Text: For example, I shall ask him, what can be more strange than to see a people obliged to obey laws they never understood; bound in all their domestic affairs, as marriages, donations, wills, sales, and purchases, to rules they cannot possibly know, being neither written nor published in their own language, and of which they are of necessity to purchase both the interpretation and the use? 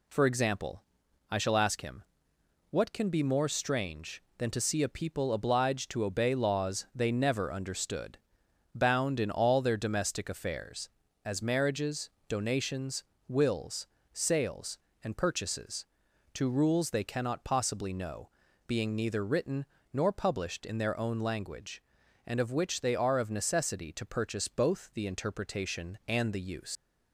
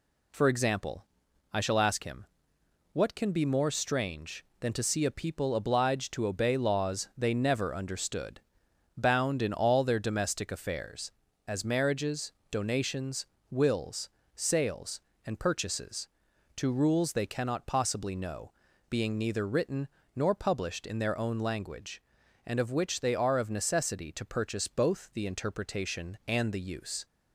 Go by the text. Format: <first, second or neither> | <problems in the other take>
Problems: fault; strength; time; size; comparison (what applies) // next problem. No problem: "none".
second | pauses between "written" and "nor"; slight; at 19.6 s; 0.28 s long; slight in the second // leaves "use" unfinished; at 26.7 s; 100 ms